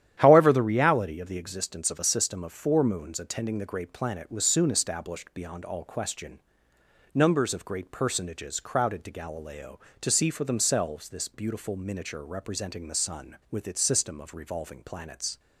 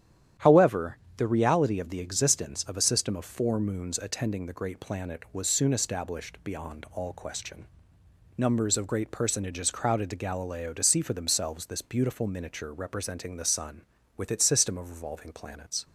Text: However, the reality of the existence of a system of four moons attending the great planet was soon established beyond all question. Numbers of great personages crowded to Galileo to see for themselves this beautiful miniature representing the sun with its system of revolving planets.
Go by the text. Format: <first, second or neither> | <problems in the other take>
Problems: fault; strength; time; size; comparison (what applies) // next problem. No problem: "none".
neither | starts louder than the rest; strong; the same in both